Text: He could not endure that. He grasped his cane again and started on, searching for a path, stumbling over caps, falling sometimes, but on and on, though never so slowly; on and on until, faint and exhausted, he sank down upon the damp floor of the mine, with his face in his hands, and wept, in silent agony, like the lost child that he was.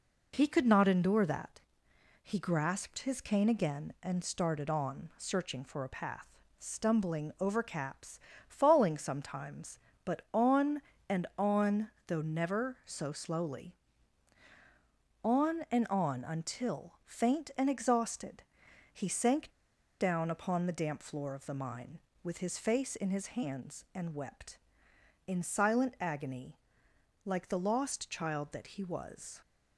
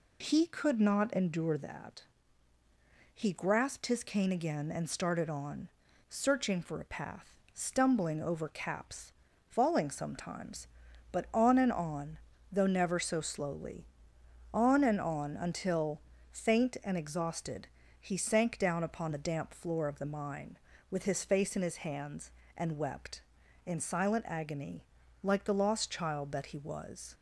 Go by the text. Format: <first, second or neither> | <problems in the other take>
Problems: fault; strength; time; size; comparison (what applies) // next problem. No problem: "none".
second | pauses between "sank" and "down"; noticeable; at 19.4 s; 0.51 s long